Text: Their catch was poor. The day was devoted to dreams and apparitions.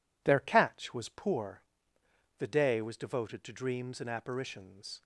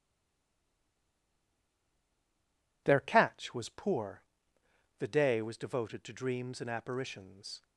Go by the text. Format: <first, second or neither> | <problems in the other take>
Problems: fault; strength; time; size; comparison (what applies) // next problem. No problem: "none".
first | stays silent before the first word; strong; until 2.8 s; 2.8 s long